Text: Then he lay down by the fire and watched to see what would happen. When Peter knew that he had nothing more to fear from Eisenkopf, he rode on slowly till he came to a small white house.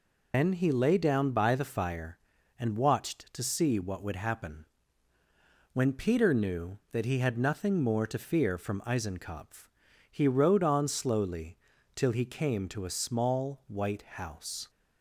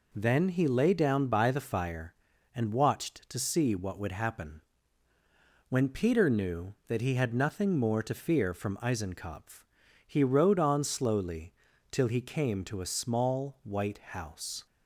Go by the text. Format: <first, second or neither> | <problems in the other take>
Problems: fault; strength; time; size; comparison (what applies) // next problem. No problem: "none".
second | loses the start of "Then"; at 0.3 s; 165 ms // pauses between "slowly" and "till"; at 11.5 s; 0.38 s long; also in the second